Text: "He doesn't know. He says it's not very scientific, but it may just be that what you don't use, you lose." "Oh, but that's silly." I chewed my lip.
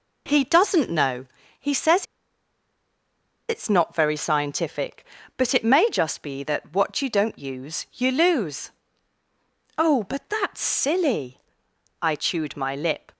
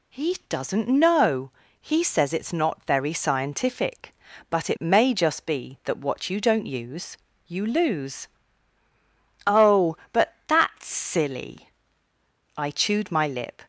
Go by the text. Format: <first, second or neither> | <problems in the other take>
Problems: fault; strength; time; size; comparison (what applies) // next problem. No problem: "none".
second | pauses between "says" and "it's"; strong; at 2.0 s; 1.4 s long